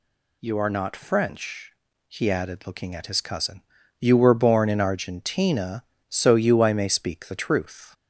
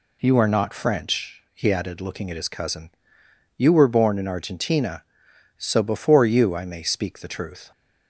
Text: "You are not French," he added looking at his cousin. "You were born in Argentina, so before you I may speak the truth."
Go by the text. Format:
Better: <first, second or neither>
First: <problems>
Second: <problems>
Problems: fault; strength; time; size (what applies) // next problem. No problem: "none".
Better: second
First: skips "before"; at 6.3 s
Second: none